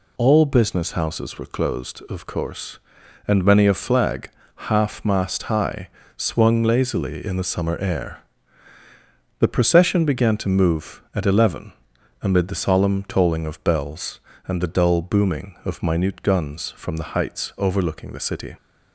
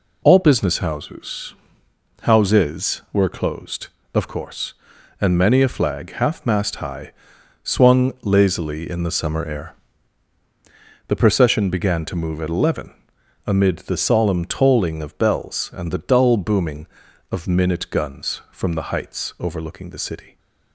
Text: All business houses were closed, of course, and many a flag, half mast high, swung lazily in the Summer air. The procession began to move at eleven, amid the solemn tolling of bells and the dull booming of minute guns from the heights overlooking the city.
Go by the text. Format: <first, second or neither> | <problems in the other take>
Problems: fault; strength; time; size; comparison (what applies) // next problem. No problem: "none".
first | says "houses" twice; at 2.2 s